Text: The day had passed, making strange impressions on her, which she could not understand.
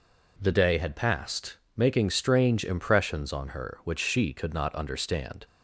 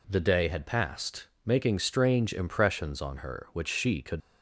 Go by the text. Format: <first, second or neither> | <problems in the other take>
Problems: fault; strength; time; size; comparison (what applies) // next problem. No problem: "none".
first | stops before "not understand"; at 4.2 s